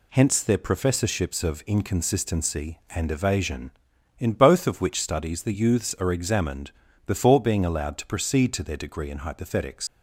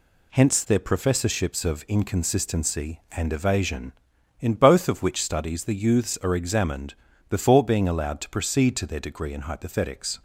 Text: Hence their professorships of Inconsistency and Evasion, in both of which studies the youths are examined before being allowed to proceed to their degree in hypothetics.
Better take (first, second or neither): second